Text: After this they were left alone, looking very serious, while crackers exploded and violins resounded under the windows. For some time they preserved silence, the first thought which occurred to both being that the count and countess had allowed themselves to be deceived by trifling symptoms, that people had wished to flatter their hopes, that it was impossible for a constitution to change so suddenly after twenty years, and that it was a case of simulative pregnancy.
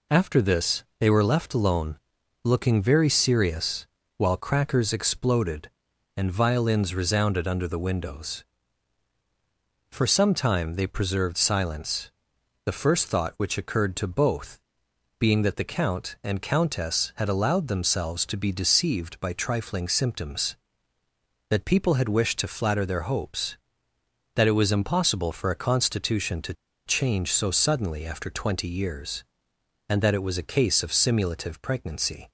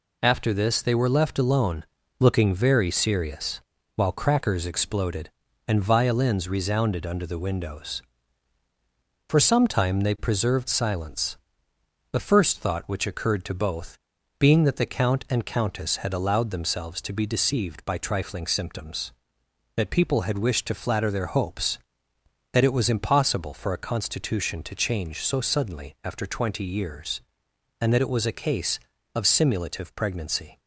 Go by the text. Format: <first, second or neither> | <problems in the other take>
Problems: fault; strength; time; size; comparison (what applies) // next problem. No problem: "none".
second | pauses between "this" and "they"; slight; at 0.8 s; 0.16 s long // pauses between "both" and "being"; noticeable; at 14.6 s; 0.58 s long; also in the second // pauses between "to" and "change"; slight; at 26.5 s; 0.33 s long